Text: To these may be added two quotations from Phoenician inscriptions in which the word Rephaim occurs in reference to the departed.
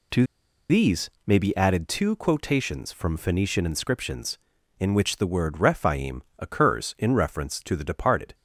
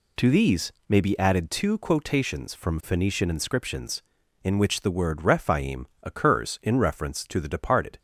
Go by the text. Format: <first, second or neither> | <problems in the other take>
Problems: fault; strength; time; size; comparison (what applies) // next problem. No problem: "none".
second | pauses between "To" and "these"; at 0.2 s; 0.45 s long // pauses between "these" and "may"; slight; at 1.0 s; 0.16 s long; slight in the second // pauses between "Rephaim" and "occurs"; slight; at 6.2 s; 0.16 s long; slight in the second